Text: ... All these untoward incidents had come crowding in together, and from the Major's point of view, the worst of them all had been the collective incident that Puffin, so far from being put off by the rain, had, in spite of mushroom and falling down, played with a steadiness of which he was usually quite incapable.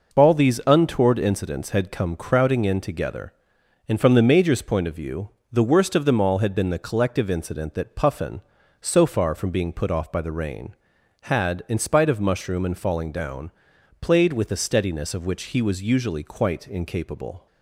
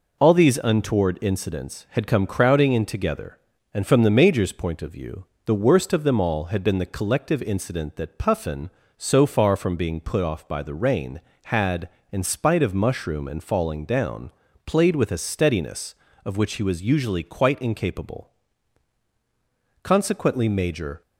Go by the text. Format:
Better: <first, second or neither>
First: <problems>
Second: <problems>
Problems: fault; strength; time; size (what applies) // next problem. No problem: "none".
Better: first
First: none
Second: goes on to say "Consequently Major"; noticeable; from 19.8 s on; 1.1 s long